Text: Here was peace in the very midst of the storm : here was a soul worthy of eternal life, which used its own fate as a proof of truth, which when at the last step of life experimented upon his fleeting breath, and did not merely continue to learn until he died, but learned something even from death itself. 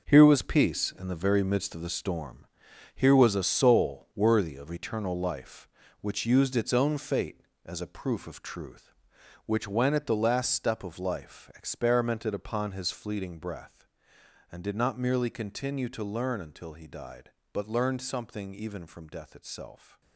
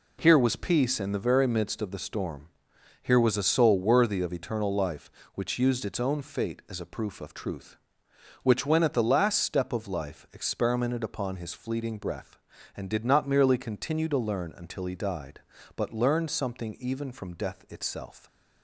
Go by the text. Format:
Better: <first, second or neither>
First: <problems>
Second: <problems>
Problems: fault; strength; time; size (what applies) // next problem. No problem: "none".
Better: second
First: gets quieter; strong; throughout; 10.5 dB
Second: none